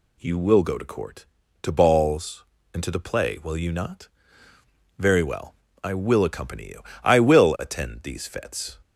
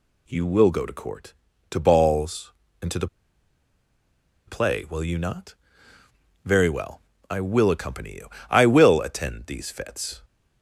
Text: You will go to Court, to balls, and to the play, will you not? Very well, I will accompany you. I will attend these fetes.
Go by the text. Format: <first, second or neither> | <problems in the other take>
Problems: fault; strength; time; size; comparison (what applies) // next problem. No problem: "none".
first | pauses between "the" and "play"; strong; at 3.0 s; 1.4 s long